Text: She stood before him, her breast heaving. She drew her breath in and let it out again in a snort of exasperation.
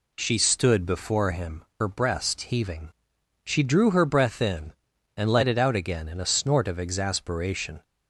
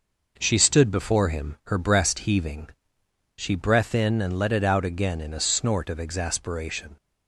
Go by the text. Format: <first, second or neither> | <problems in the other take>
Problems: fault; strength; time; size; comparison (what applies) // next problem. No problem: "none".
first | skips "drew her"; at 3.5 s